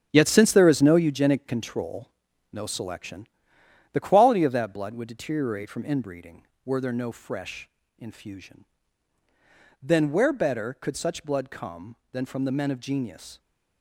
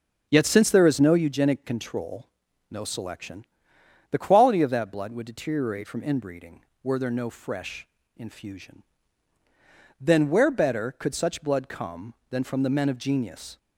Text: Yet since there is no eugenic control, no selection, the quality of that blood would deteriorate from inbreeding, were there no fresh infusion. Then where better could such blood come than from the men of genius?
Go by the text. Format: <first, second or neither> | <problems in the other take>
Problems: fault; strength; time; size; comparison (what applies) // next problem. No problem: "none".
second | gets quieter; strong; throughout; 8.5 dB // pauses between "fresh" and "infusion"; slight; at 7.6 s; 0.30 s long; slight in the second